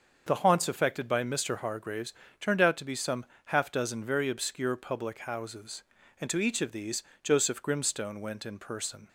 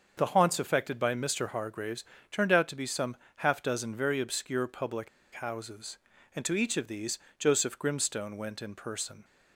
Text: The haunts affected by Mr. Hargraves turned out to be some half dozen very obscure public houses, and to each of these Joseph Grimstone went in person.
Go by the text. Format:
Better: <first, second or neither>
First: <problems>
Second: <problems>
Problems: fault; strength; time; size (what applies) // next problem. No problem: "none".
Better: first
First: starts louder than the rest; until 1.2 s; 6.5 dB // pauses between "Hargraves" and "turned"; slight; at 2.1 s; 0.30 s long // pauses between "some" and "half"; slight; at 3.2 s; 0.22 s long // pauses between "these" and "Joseph"; slight; at 7.0 s; 0.18 s long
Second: starts louder than the rest; until 1.1 s; 6.5 dB // pauses between "Hargraves" and "turned"; slight; at 2.0 s; 0.30 s long // pauses between "some" and "half"; slight; at 3.1 s; 0.22 s long // pauses between "public" and "houses"; slight; at 5.0 s; 0.25 s long // pauses between "these" and "Joseph"; slight; at 7.2 s; 0.18 s long